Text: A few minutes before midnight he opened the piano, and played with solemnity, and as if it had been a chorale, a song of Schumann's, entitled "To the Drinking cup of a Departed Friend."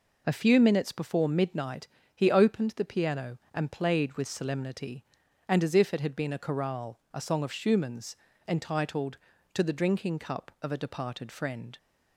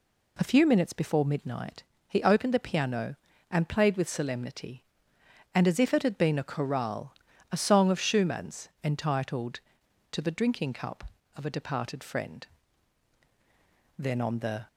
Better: first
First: pauses between "midnight" and "he"; slight; at 1.8 s; 0.30 s long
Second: pauses between "midnight" and "he"; slight; at 1.8 s; 0.26 s long // goes on to say "Then on the"; noticeable; from 13.9 s on; 0.70 s long

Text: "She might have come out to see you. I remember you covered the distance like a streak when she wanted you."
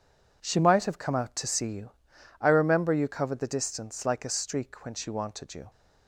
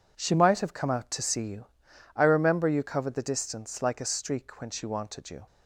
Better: neither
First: none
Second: none

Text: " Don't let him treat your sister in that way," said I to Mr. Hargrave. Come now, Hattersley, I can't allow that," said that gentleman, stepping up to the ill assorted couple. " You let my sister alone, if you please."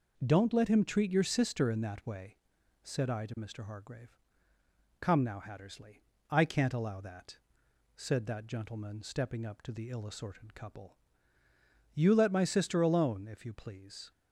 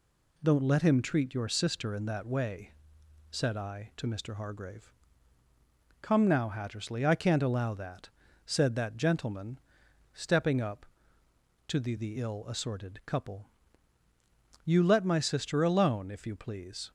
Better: first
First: none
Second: says "the" twice; at 11.9 s

